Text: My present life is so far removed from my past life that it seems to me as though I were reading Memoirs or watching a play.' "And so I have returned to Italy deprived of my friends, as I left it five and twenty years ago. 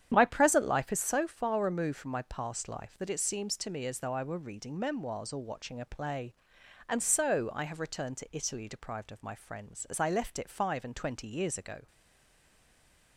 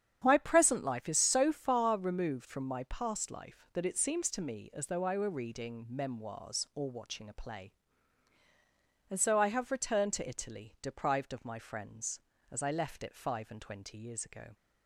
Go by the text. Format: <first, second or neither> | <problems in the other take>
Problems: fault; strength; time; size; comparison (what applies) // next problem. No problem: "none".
second | starts louder than the rest; strong; until 1.1 s; 9.5 dB; strong in the second // stays silent after the last word; noticeable; from 11.8 s on; 1.3 s long